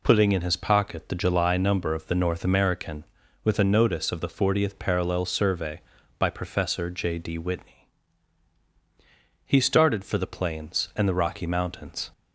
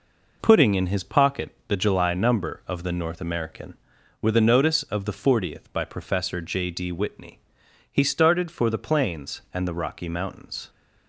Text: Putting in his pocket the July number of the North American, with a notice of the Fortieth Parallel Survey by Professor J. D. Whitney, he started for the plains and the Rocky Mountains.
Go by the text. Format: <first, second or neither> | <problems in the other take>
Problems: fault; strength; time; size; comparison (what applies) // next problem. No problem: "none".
first | skips "Parallel Survey"; at 5.7 s